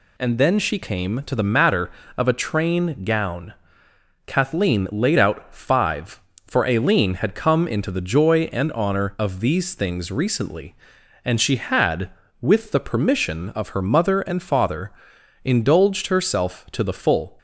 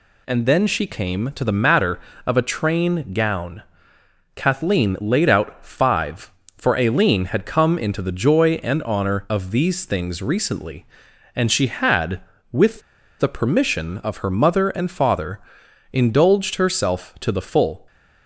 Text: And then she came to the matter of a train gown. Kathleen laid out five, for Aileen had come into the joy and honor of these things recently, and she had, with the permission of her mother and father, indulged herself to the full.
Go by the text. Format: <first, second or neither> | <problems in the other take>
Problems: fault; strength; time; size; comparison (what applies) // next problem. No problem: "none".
first | pauses between "with" and "the"; at 12.8 s; 0.38 s long